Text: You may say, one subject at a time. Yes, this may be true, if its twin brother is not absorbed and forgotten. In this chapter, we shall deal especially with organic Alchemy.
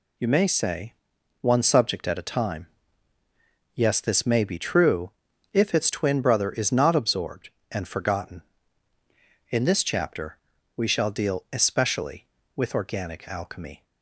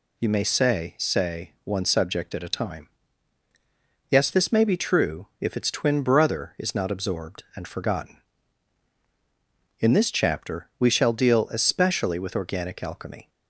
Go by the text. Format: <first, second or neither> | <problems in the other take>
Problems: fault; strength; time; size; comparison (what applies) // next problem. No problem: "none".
first | says "say" twice; at 0.9 s